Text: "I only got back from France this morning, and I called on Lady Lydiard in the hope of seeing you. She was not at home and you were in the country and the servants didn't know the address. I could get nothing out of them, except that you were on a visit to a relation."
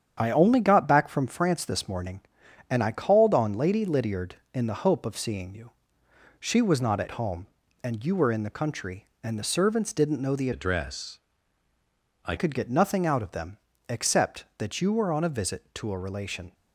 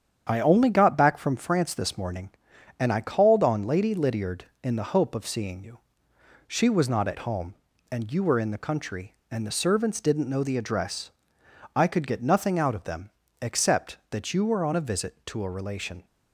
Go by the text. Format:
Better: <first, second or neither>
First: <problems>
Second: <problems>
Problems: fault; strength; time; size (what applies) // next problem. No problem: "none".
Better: second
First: starts louder than the rest; strong; until 1.1 s; 8.5 dB // changes voice from "address" to "I"; from 10.5 to 12.3 s; 1.8 s long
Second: starts louder than the rest; strong; until 1.2 s; 8.5 dB